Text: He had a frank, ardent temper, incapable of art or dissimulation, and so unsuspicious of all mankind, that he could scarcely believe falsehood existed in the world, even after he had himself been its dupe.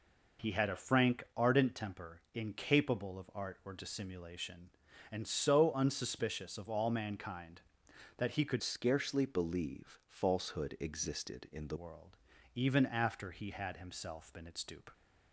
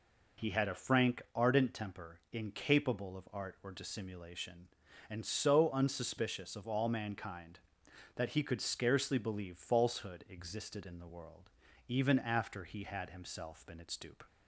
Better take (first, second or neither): second